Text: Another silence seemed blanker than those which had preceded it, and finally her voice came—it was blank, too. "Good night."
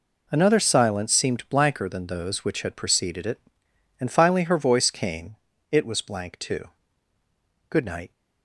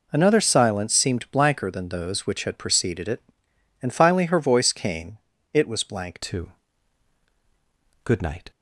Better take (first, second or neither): first